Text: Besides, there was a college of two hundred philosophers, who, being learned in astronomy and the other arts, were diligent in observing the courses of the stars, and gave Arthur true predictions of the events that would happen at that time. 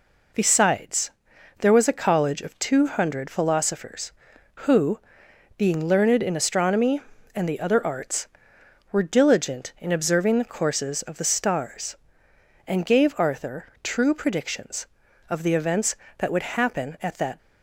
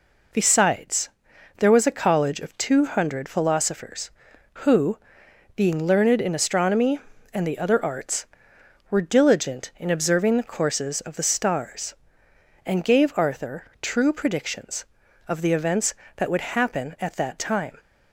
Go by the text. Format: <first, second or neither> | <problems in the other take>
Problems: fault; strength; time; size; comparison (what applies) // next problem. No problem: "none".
second | pauses between "Arthur" and "true"; slight; at 13.6 s; 0.16 s long; slight in the second // stops before "time"; at 17.3 s